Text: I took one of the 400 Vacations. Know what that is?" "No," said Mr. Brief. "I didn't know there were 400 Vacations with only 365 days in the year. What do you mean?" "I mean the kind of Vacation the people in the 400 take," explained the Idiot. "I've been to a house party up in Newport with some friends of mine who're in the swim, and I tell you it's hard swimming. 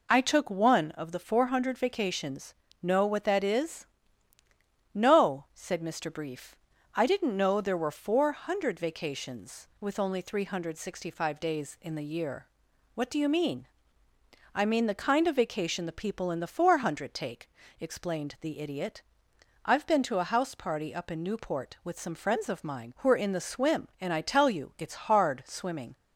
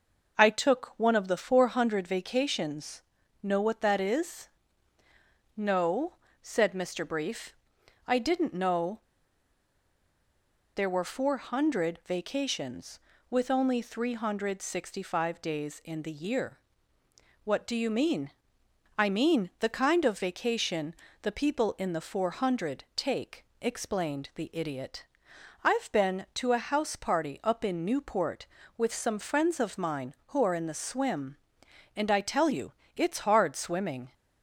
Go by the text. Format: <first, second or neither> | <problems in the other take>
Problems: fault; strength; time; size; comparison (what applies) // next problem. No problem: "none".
first | pauses between "know" and "there"; strong; at 8.9 s; 1.7 s long // pauses between "Vacation" and "the"; slight; at 20.9 s; 0.26 s long // pauses between "you" and "it's"; slight; at 32.7 s; 0.24 s long